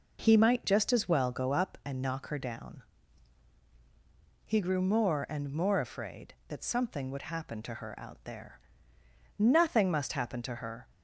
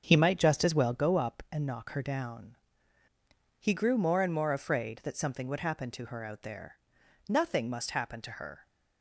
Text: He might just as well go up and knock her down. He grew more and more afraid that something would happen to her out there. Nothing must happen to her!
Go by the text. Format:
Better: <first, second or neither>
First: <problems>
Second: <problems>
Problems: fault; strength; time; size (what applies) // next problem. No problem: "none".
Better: first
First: none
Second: starts louder than the rest; until 1.0 s; 7 dB